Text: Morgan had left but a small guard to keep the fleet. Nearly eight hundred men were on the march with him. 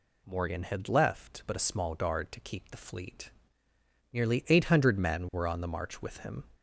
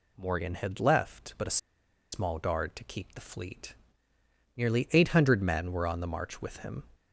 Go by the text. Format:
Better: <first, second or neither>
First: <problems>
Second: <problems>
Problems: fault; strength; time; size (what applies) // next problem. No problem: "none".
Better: first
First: none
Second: pauses between "a" and "small"; noticeable; at 1.5 s; 0.55 s long